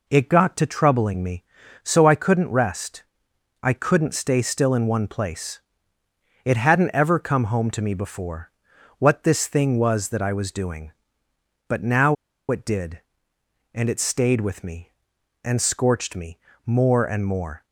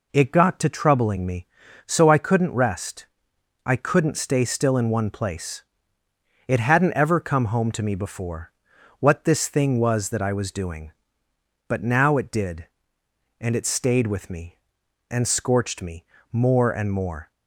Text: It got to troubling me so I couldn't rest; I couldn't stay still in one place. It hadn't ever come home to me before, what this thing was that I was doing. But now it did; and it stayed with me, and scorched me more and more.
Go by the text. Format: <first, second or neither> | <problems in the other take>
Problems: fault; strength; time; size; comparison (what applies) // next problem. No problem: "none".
second | pauses between "now" and "it"; slight; at 12.1 s; 0.35 s long // pauses between "me" and "more"; slight; at 16.3 s; 0.26 s long; slight in the second